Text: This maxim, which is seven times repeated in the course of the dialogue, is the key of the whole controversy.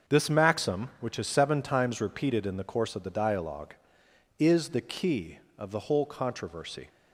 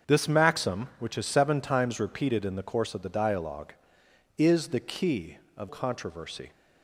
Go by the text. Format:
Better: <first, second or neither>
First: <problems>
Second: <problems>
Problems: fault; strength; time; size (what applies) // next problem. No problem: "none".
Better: first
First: starts louder than the rest; noticeable; until 1.1 s; 6 dB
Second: starts louder than the rest; until 1.1 s; 6.5 dB // skips "the whole"; at 5.6 s